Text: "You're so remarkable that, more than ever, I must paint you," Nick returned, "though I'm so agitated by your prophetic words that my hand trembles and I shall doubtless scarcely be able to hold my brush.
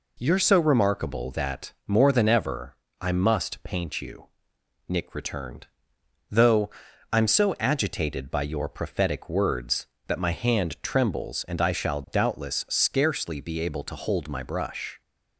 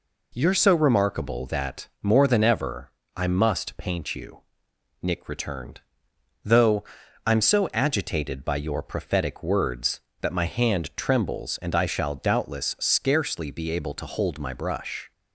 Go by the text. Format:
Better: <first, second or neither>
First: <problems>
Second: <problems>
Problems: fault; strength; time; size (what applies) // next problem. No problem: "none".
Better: neither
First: pauses between "though" and "I'm"; at 6.7 s; 0.42 s long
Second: pauses between "though" and "I'm"; at 6.8 s; 0.42 s long